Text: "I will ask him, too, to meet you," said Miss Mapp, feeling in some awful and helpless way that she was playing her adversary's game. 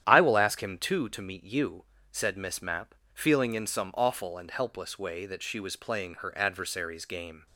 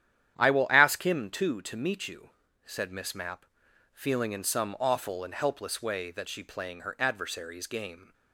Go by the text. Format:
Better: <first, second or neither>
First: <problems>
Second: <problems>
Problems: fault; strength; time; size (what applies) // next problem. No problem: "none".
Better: first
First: starts louder than the rest; strong; until 1.0 s; 10.5 dB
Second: starts louder than the rest; strong; until 1.3 s; 10 dB // skips "was"; at 6.4 s